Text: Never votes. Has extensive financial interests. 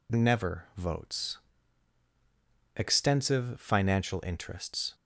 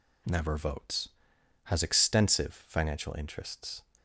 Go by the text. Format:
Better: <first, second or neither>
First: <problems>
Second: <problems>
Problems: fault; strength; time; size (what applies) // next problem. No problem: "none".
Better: second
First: skips "Has"; at 2.0 s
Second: none